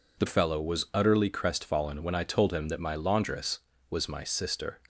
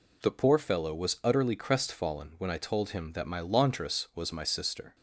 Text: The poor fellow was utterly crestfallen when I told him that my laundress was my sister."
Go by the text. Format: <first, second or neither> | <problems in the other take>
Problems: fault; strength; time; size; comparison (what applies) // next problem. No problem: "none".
second | skips "poor"; at 0.2 s